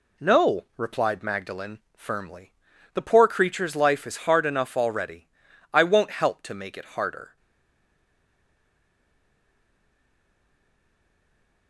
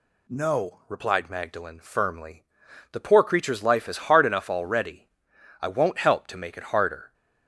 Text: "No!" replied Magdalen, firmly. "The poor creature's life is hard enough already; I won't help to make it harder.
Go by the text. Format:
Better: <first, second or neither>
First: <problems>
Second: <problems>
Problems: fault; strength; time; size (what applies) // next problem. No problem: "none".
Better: second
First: stays silent after the last word; strong; from 7.3 s on; 4.3 s long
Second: none